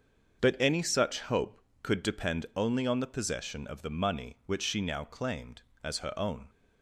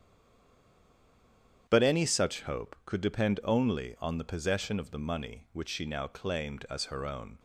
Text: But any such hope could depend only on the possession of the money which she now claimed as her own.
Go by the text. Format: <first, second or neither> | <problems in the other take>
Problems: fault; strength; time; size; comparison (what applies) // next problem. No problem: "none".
first | stays silent before the first word; noticeable; until 1.6 s; 1.6 s long // starts louder than the rest; strong; until 2.6 s; 9 dB; also in the first